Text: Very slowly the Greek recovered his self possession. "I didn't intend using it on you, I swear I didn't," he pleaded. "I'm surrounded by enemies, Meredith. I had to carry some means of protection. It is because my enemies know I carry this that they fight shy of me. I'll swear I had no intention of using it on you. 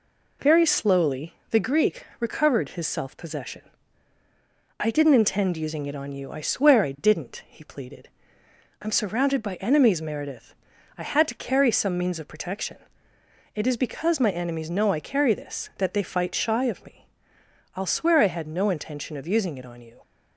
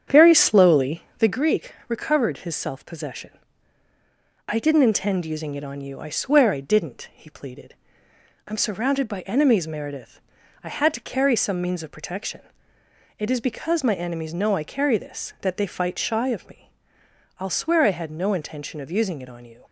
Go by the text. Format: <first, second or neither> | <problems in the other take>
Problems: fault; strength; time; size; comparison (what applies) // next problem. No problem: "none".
first | starts louder than the rest; strong; until 1.3 s; 8 dB // pauses between "slowly" and "the"; slight; at 1.0 s; 0.16 s long; slight in the first // pauses between "Greek" and "recovered"; slight; at 1.7 s; 0.16 s long; slight in the first